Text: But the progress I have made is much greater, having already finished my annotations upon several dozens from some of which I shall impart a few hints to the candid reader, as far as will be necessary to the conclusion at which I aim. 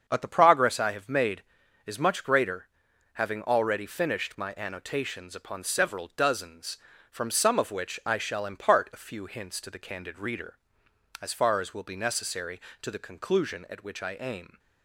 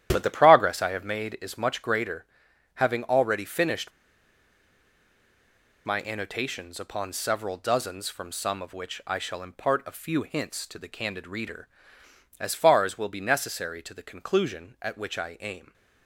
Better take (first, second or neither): first